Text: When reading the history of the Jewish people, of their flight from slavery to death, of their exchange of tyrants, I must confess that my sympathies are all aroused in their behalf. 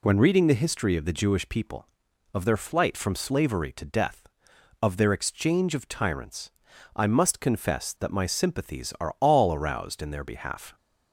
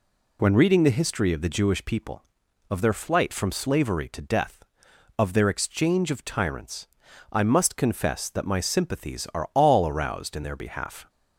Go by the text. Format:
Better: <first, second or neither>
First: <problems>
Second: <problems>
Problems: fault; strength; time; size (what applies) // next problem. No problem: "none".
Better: neither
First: none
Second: none